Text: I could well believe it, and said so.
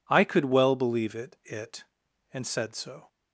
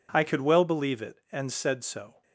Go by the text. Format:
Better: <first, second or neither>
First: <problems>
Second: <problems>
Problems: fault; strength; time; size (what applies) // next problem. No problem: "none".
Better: second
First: says "it" twice; at 1.4 s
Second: none